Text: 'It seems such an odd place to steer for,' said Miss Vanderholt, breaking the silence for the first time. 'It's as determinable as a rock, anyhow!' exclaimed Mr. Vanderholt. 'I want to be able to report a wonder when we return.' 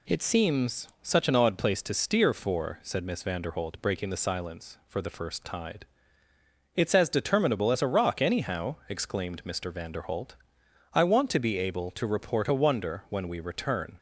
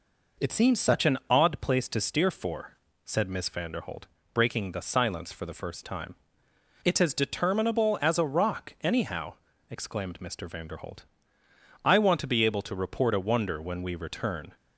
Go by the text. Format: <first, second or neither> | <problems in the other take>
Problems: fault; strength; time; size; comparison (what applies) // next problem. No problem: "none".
second | pauses between "seems" and "such"; slight; at 0.8 s; 0.16 s long // says "tide" for "time"; at 5.4 s